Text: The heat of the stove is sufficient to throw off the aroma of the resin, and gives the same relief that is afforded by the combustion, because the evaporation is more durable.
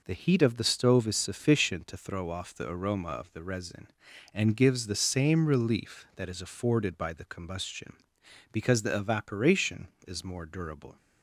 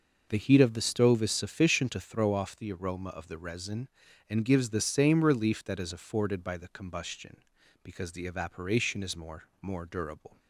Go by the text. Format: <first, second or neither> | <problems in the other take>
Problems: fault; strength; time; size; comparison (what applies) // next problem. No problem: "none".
first | says "more" twice; at 9.6 s